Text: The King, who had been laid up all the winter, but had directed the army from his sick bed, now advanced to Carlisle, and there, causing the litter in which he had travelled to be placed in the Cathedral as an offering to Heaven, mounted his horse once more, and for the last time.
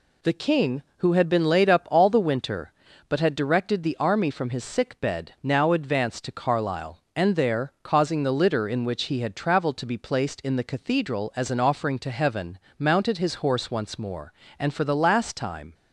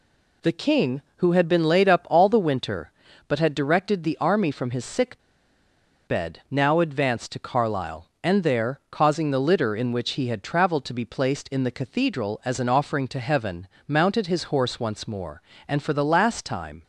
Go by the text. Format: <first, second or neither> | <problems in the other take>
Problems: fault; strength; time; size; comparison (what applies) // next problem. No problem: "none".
first | pauses between "sick" and "bed"; noticeable; at 5.1 s; 0.87 s long